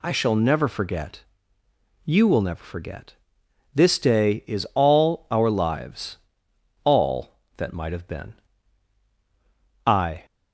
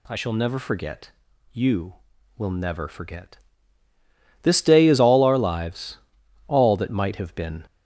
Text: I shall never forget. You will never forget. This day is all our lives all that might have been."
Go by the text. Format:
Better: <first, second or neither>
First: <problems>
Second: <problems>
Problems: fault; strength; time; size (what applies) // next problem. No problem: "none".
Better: second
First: pauses between "lives" and "all"; noticeable; at 6.1 s; 0.69 s long // goes on to say "I"; slight; from 9.8 s on; 0.38 s long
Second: pauses between "lives" and "all"; noticeable; at 5.9 s; 0.48 s long